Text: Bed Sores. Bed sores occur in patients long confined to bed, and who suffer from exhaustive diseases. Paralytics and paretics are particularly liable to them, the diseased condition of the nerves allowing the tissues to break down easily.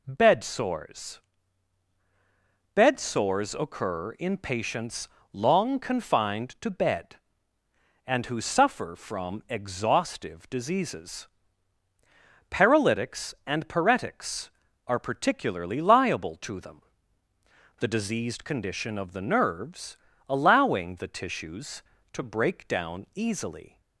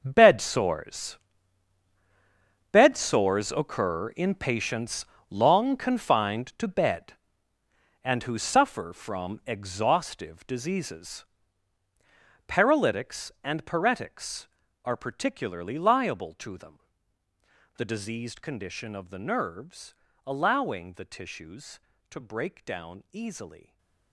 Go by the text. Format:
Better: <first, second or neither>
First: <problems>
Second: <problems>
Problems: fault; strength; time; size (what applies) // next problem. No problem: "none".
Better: first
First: pauses between "patients" and "long"; slight; at 5.0 s; 0.24 s long // pauses between "nerves" and "allowing"; slight; at 19.9 s; 0.32 s long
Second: gets quieter; strong; throughout; 14.5 dB // pauses between "patients" and "long"; slight; at 5.0 s; 0.24 s long // pauses between "nerves" and "allowing"; slight; at 19.9 s; 0.32 s long // stays silent after the last word; slight; from 23.6 s on; 0.5 s long